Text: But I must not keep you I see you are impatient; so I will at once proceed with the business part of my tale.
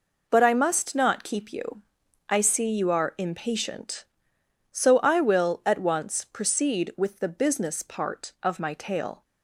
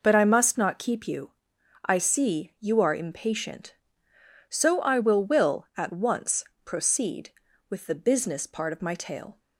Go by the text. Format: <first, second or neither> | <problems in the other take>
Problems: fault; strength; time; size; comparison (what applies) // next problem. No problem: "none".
first | pauses between "you" and "I"; noticeable; at 1.3 s; 0.54 s long; noticeable in the first // says "will" twice; at 5.2 s // pauses between "once" and "proceed"; slight; at 6.4 s; 0.18 s long